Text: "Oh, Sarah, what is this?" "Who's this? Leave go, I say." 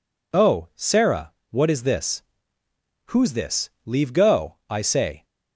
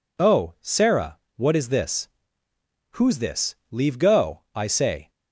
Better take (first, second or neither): neither